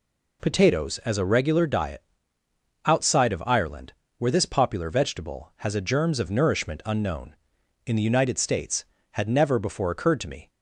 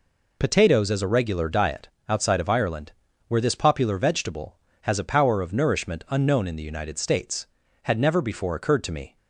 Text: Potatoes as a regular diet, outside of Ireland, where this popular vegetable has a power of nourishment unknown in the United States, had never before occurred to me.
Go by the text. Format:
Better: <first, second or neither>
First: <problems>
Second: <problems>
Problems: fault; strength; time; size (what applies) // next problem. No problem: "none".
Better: second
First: says "germs" for "power"; at 5.8 s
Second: none